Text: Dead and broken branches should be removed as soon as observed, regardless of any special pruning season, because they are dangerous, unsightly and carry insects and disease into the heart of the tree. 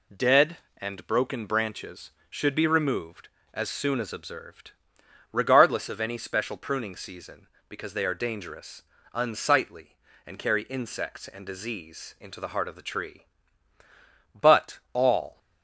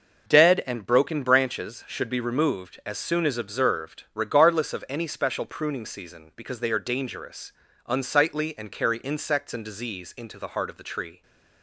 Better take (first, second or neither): second